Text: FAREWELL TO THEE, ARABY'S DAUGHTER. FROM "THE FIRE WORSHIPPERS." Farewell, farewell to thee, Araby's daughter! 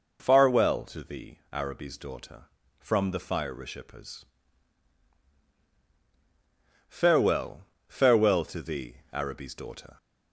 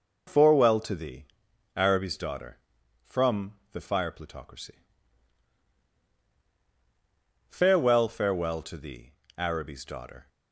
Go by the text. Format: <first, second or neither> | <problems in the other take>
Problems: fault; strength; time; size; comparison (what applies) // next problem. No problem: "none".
first | pauses between "FROM" and "THE"; slight; at 3.5 s; 0.18 s long // says "Plutocracy" for "WORSHIPPERS"; at 4.1 s